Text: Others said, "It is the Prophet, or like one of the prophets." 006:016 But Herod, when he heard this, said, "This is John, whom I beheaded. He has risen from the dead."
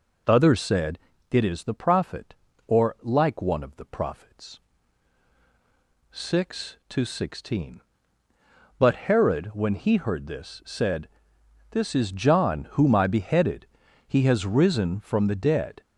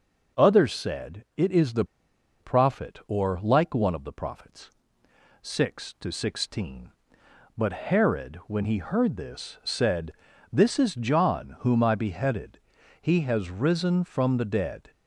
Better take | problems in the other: first | pauses between "the" and "Prophet"; noticeable; at 1.8 s; 0.55 s long

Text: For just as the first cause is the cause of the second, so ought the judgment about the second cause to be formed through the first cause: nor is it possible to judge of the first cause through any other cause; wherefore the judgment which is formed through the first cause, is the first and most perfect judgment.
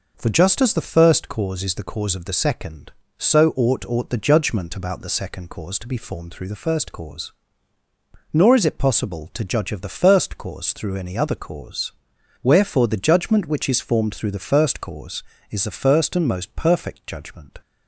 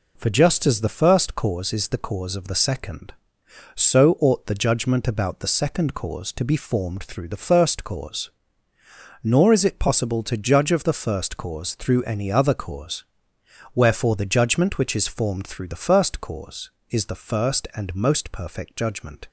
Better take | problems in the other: second | says "ought" twice; at 3.8 s

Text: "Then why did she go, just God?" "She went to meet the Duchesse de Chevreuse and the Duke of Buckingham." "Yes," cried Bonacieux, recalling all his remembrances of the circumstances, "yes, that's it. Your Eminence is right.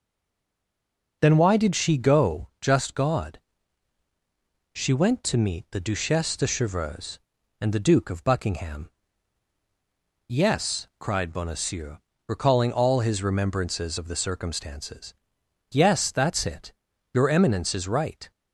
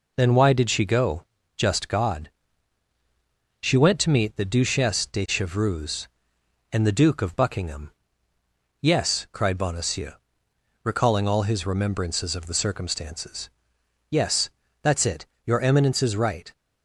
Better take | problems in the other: second | stays silent before the first word; noticeable; until 1.2 s; 1.2 s long

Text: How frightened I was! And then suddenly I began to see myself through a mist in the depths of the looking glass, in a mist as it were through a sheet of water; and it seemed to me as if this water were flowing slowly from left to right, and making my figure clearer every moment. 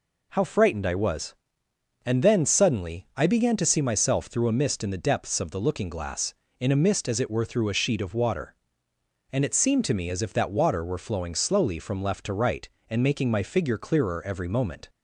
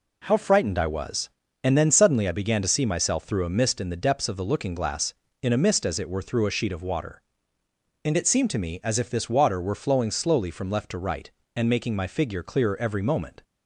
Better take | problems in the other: second | says "that" for "this"; at 10.3 s

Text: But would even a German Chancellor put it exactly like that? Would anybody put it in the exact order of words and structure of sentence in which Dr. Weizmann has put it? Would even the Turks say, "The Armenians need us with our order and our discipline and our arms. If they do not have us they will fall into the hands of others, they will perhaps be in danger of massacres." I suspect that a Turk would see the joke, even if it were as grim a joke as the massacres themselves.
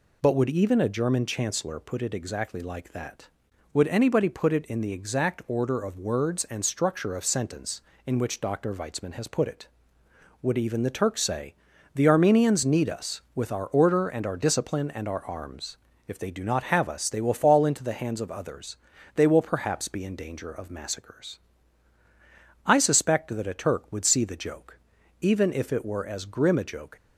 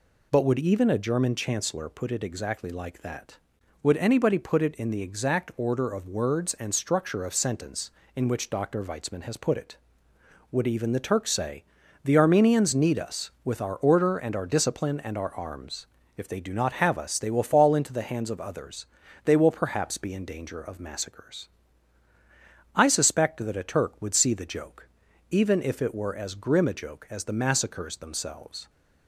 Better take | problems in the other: second | stops before "as the massacres themselves"; at 26.9 s

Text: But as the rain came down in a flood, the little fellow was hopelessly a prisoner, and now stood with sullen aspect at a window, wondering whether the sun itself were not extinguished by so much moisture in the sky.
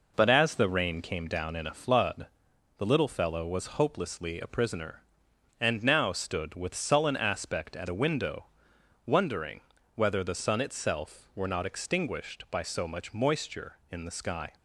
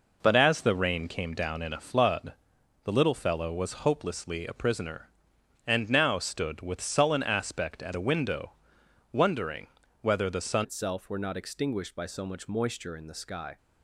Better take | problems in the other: first | pauses between "wondering" and "whether"; slight; at 9.6 s; 0.34 s long; slight in the first // changes voice at "itself"; from 10.6 s on; 2.9 s long

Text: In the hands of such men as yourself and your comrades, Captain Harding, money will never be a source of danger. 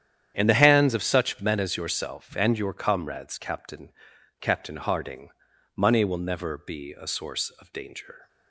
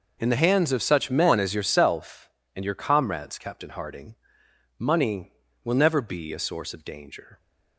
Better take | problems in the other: second | starts louder than the rest; strong; until 1.3 s; 9.5 dB // says "Captain" twice; at 4.4 s

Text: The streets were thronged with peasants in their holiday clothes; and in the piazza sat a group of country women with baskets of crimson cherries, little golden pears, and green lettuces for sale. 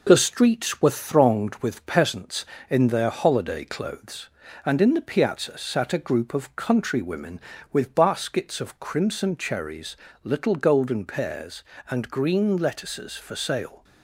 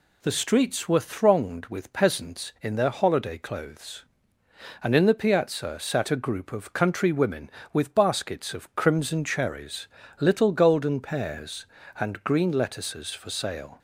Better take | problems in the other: second | gets quieter; slight; throughout; 3 dB

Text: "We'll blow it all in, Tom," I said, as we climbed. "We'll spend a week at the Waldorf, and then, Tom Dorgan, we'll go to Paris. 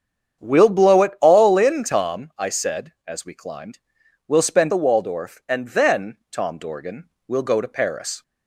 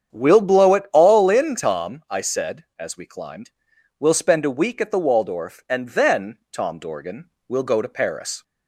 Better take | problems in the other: second | starts louder than the rest; strong; until 1.4 s; 8 dB; strong in the second // skips "a week at"; at 4.7 s

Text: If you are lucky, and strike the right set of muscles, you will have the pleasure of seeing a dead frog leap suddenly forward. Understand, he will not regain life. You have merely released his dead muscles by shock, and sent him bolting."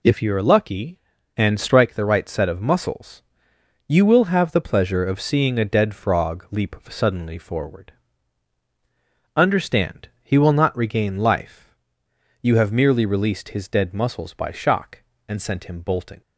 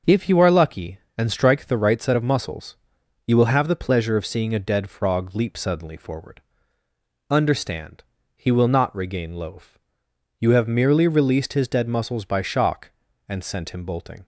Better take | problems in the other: first | says "loaf" for "life"; at 9.3 s

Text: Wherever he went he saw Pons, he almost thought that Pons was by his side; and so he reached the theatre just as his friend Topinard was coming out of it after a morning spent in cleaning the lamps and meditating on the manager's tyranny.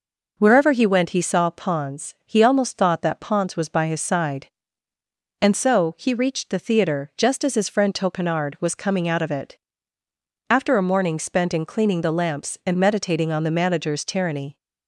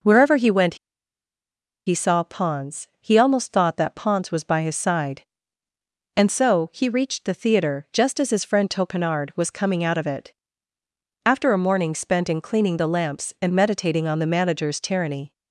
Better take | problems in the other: first | pauses between "went" and "he"; at 0.7 s; 1.1 s long // pauses between "it" and "after"; noticeable; at 10.3 s; 0.94 s long; noticeable in the first

